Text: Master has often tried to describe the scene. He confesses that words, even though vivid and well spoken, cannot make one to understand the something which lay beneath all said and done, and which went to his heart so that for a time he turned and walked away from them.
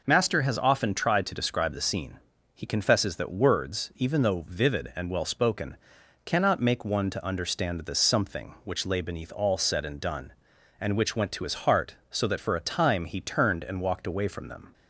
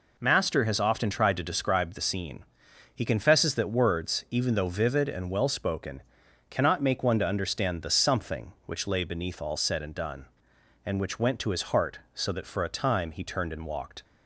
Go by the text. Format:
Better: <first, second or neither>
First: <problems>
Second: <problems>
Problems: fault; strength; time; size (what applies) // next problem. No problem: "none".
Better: first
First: none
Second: stops before "away from them"; at 14.0 s